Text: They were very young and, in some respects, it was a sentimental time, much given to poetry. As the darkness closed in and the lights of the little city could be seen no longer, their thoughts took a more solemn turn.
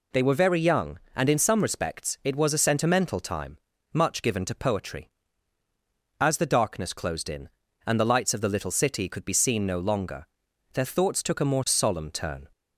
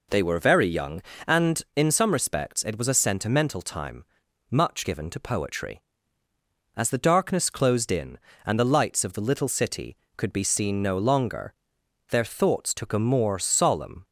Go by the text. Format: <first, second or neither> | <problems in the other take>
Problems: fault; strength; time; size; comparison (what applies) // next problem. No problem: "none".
first | stops before "turn"; at 14.0 s